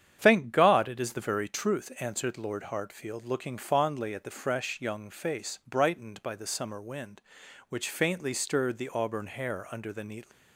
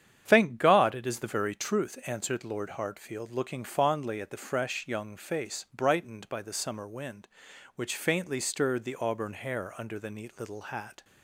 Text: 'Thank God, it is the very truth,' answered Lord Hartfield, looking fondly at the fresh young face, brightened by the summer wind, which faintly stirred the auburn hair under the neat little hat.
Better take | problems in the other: second | starts louder than the rest; strong; until 1.2 s; 9 dB; strong in the second // stops before "little hat"; at 10.3 s

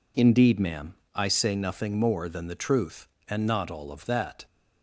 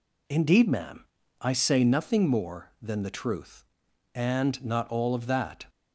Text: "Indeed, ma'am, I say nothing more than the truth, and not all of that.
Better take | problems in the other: neither | none

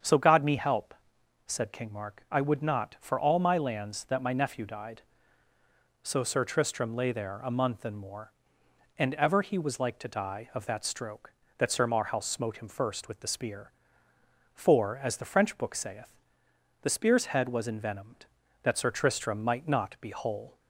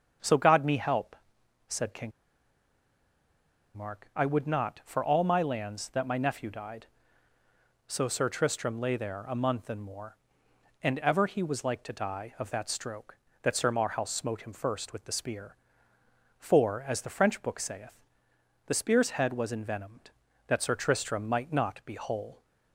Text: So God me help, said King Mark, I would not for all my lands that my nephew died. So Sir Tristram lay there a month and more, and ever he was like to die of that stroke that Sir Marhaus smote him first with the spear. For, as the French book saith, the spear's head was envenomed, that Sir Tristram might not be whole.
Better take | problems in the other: first | starts louder than the rest; strong; until 1.7 s; 7 dB; strong in the first // pauses between "King" and "Mark"; strong; at 2.1 s; 1.6 s long

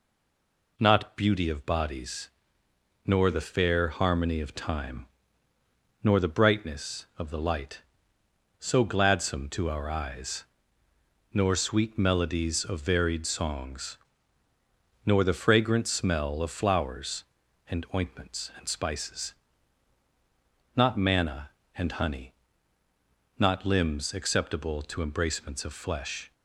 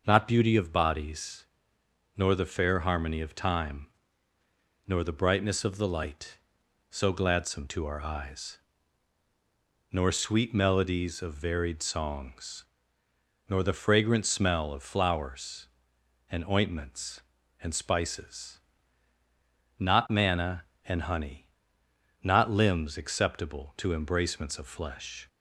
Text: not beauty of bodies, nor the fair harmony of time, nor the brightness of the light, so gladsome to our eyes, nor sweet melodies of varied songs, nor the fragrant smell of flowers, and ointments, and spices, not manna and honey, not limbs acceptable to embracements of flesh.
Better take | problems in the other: second | stays silent before the first word; slight; until 0.7 s; 0.7 s long

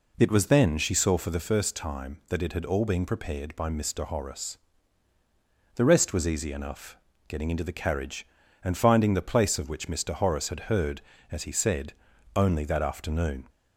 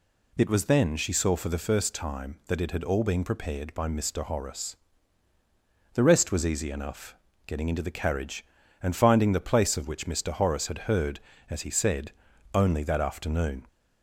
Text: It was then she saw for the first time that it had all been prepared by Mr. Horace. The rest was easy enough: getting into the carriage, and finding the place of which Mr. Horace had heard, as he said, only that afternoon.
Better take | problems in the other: second | starts louder than the rest; until 1.3 s; 3.5 dB

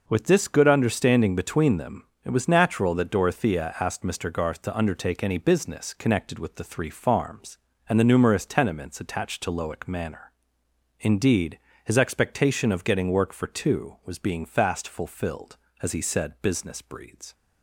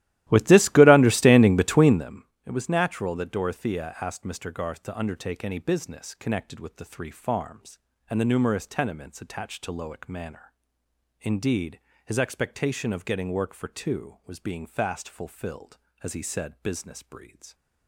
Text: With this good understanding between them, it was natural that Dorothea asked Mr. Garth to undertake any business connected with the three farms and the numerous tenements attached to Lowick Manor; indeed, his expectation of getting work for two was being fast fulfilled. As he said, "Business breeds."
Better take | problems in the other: first | starts louder than the rest; strong; until 2.2 s; 15 dB

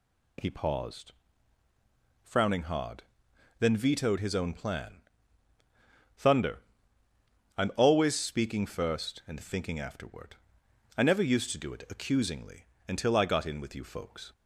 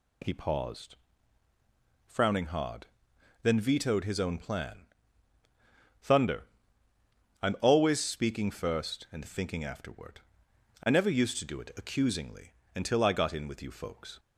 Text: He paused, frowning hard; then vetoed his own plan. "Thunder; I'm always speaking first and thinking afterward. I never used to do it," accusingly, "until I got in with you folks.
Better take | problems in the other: neither | none

